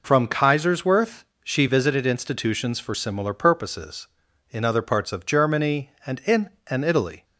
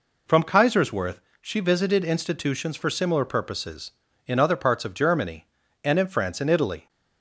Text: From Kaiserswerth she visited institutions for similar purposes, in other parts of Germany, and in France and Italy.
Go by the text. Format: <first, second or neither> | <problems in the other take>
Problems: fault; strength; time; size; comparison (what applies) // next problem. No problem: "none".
second | pauses between "Kaiserswerth" and "she"; slight; at 1.2 s; 0.20 s long; slight in the second // skips "France"; at 6.5 s